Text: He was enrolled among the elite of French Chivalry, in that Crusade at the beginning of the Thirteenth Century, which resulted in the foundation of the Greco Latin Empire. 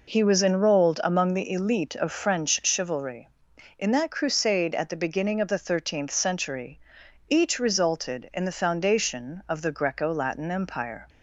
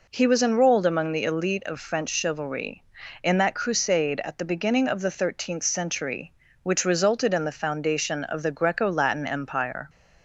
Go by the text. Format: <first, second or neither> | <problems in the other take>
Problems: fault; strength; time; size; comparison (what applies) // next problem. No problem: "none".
second | says "each" for "which"; at 7.2 s